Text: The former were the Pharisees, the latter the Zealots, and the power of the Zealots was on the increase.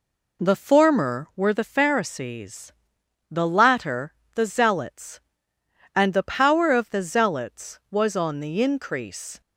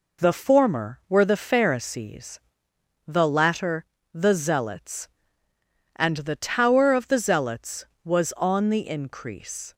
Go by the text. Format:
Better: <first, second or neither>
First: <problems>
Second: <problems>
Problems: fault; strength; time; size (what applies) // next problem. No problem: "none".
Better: first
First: pauses between "latter" and "the"; slight; at 4.1 s; 0.22 s long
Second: pauses between "latter" and "the"; slight; at 3.8 s; 0.28 s long // says "tower" for "power"; at 6.3 s